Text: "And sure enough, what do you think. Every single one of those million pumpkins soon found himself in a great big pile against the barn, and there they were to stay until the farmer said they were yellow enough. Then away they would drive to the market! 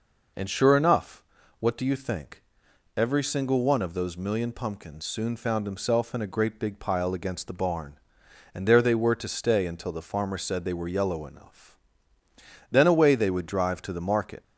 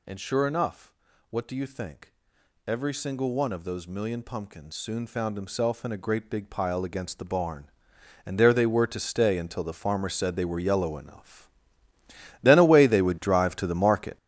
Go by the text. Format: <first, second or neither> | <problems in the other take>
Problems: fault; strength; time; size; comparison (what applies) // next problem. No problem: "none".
first | gets louder; strong; throughout; 10.5 dB